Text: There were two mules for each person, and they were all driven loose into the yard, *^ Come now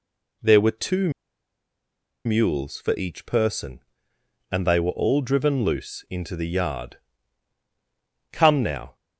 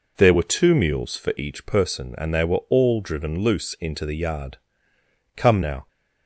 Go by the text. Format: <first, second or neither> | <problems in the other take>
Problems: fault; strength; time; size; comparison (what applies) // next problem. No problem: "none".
second | pauses between "two" and "mules"; at 1.1 s; 1.1 s long